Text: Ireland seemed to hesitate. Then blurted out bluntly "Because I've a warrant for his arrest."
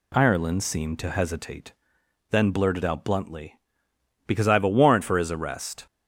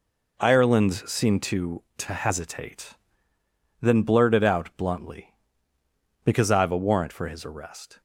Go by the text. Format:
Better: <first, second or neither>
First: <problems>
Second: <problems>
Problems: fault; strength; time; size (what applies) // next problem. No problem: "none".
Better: first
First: none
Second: says "to" twice; at 1.9 s